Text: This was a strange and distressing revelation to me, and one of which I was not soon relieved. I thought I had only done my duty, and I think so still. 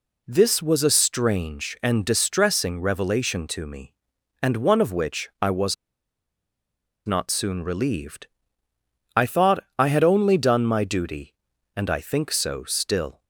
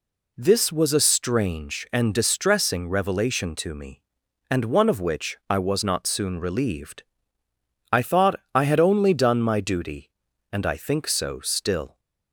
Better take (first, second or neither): second